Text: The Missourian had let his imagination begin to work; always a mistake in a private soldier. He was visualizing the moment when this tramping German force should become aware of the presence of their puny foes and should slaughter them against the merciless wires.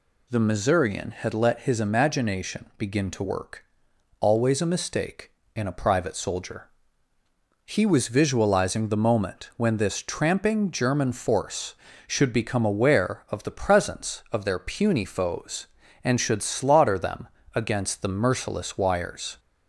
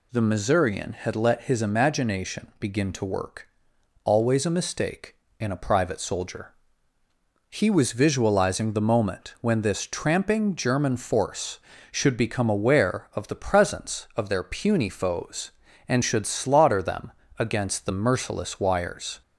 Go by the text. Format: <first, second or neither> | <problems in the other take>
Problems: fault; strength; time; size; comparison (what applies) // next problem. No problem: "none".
neither | pauses between "them" and "against"; slight; the same in both